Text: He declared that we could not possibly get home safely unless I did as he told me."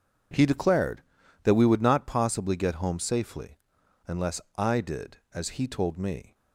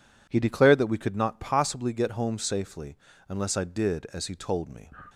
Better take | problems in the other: second | says "would" for "could"; at 1.6 s // pauses between "safely" and "unless"; noticeable; at 3.5 s; 0.50 s long; slight in the second // pauses between "unless" and "I"; slight; at 4.4 s; 0.16 s long

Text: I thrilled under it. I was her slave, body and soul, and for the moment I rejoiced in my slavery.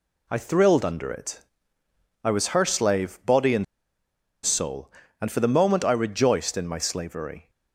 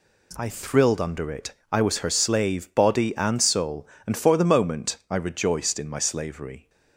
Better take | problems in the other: second | pauses between "and" and "soul"; noticeable; at 3.6 s; 0.78 s long

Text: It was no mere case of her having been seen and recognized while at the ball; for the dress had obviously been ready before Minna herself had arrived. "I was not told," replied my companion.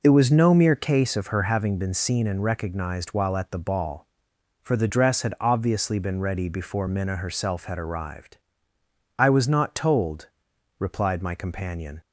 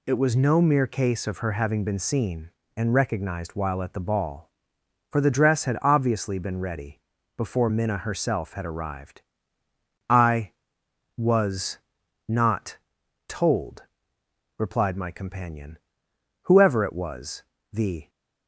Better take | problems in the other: first | pauses between "ready" and "before"; at 6.9 s; 0.38 s long // pauses between "was" and "not"; noticeable; at 11.7 s; 0.50 s long // pauses between "not" and "told"; noticeable; at 12.7 s; 0.48 s long // goes on to say "Whoever it was the"; from 16.4 s on; 1.6 s long

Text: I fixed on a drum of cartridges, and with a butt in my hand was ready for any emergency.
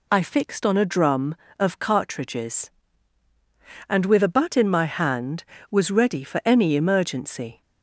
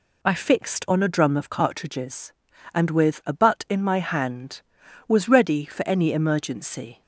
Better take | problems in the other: neither | none

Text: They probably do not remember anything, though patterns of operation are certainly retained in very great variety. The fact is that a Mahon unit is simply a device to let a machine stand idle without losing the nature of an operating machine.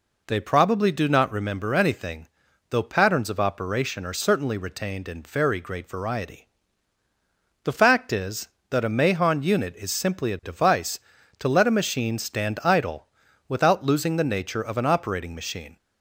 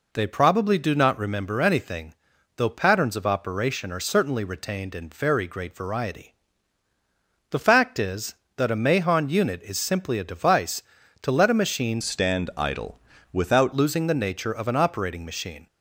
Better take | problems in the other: first | changes voice from "stand" to "without"; from 12.0 to 13.7 s; 1.7 s long // pauses between "idle" and "without"; slight; at 12.9 s; 0.36 s long; also in the first

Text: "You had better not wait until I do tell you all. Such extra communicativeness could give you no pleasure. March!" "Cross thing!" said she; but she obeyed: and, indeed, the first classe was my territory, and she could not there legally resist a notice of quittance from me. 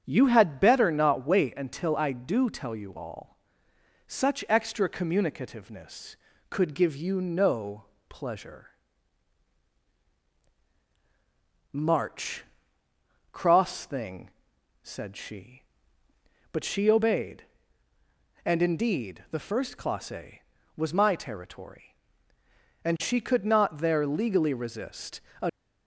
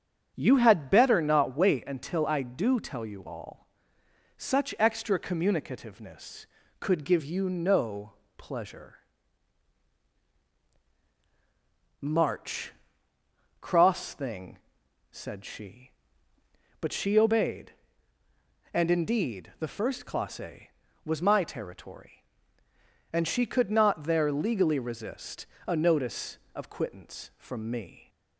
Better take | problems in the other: second | starts louder than the rest; strong; until 1.0 s; 8 dB; strong in the second // pauses between "no" and "pleasure"; slight; at 7.8 s; 0.26 s long; slight in the second // pauses between "resist" and "a"; slight; at 25.1 s; 0.22 s long; slight in the second // stops before "notice of quittance from me"; at 25.4 s

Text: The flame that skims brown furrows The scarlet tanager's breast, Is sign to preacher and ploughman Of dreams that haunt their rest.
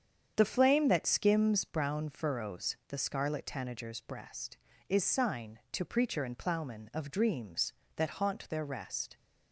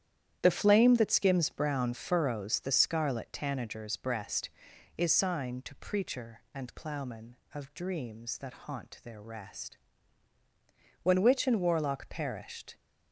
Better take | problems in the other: first | starts louder than the rest; strong; until 1.4 s; 10.5 dB; strong in the first // goes on to say "When witch and warlock perished"; strong; from 11.0 s on; 1.7 s long

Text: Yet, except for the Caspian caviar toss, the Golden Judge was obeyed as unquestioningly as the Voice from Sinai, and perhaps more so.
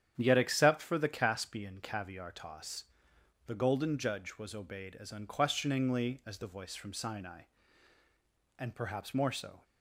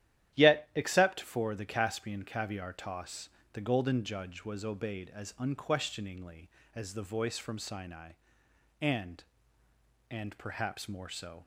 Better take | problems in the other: first | starts louder than the rest; strong; until 1.4 s; 12 dB; strong in the first // says "and" twice; at 10.0 s

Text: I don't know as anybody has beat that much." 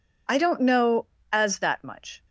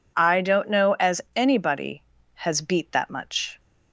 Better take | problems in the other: second | skips "anybody has beat"; at 1.5 s

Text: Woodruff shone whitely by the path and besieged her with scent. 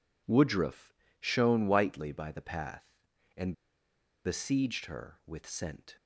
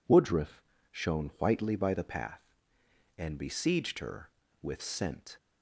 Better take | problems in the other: second | pauses between "Woodruff" and "shone"; slight; at 0.9 s; 0.26 s long; slight in the second // pauses between "and" and "besieged"; noticeable; at 3.5 s; 0.73 s long

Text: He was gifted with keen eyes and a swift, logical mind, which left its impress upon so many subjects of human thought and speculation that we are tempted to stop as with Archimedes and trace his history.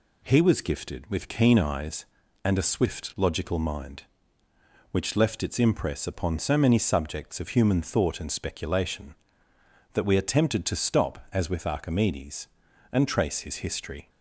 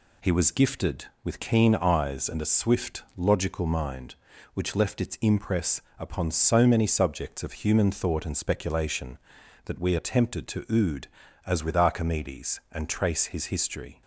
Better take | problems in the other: first | pauses between "impress" and "upon"; slight; at 5.8 s; 0.18 s long // says "ood" for "stop"; at 10.6 s

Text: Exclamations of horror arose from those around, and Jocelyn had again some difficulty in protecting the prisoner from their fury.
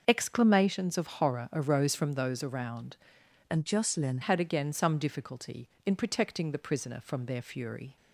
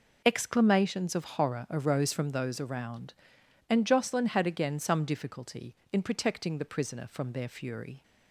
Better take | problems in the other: second | starts louder than the rest; until 1.0 s; 6.5 dB // changes voice from "and" to "Jocelyn"; from 3.5 to 4.1 s; 0.6 s long

